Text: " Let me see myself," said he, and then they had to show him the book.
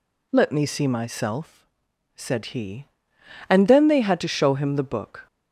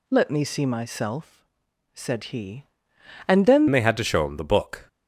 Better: first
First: none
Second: changes voice at "they"; from 3.6 s on; 1.2 s long

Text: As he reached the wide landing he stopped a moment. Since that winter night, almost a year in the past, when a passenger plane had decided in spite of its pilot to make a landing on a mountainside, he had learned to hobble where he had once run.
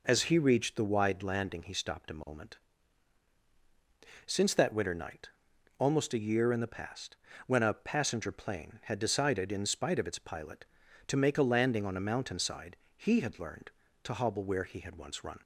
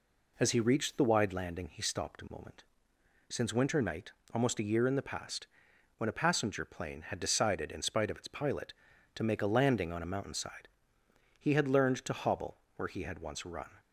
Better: first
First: none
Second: skips "that"; at 3.5 s // pauses between "hobble" and "where"; slight; at 12.5 s; 0.18 s long

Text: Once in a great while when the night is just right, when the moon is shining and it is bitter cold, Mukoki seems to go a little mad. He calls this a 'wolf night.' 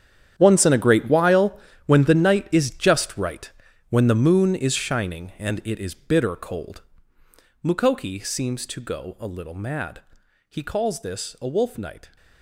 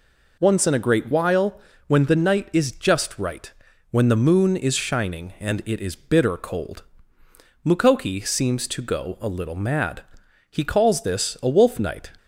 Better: second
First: gets quieter; strong; throughout; 14.5 dB // pauses between "while" and "when"; slight; at 1.5 s; 0.28 s long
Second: pauses between "while" and "when"; slight; at 1.5 s; 0.28 s long

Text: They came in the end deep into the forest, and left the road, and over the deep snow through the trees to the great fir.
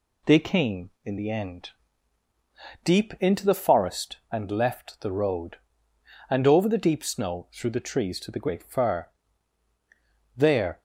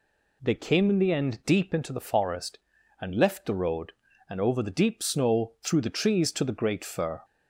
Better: second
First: pauses between "end" and "deep"; at 1.6 s; 1.1 s long // goes on to say "There"; slight; from 10.3 s on; 0.46 s long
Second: none

